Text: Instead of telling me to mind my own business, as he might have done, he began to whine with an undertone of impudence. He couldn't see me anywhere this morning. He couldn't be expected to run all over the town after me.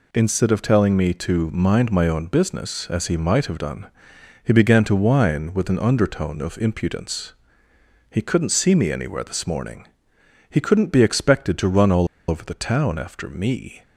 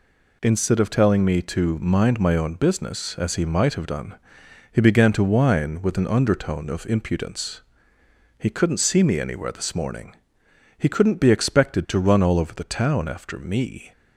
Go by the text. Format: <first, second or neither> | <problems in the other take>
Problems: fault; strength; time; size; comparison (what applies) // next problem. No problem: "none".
second | pauses between "all" and "over"; slight; at 12.0 s; 0.22 s long